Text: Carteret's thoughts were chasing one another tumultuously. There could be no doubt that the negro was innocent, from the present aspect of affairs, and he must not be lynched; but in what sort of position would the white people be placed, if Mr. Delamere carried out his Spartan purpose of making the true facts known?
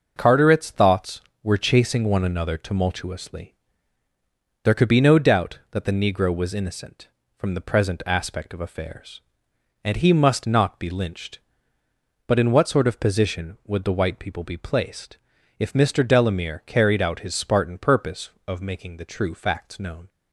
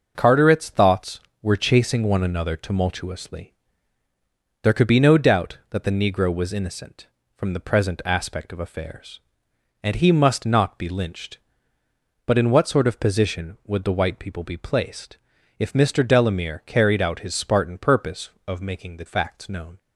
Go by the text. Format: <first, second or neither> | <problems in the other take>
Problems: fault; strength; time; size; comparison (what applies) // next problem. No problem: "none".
first | starts louder than the rest; noticeable; until 1.1 s; 6 dB; also in the first // skips "true"; at 19.0 s